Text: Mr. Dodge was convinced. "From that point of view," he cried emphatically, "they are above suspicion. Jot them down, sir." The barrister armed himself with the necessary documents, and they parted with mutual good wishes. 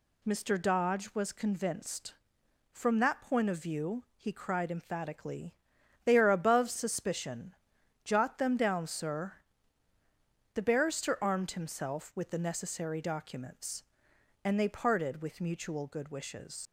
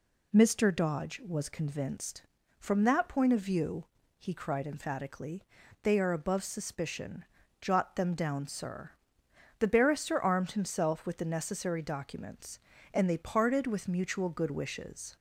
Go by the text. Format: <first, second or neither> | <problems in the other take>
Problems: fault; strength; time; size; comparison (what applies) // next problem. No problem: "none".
second | leaves "wishes" unfinished; at 16.6 s; 95 ms